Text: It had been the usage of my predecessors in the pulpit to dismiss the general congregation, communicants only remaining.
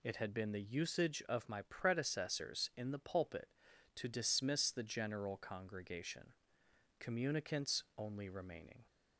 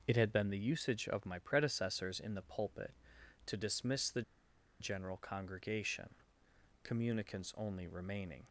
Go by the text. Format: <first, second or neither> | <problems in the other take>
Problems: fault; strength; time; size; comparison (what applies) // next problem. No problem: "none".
first | pauses between "the" and "general"; noticeable; at 4.2 s; 0.58 s long